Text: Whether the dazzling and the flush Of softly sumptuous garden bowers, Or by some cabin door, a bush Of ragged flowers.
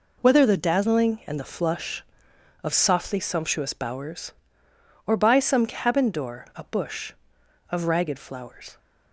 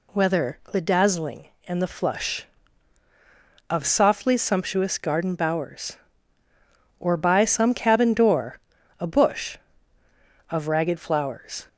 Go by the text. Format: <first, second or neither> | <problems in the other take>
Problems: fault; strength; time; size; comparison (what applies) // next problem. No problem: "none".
second | skips "garden"; at 3.7 s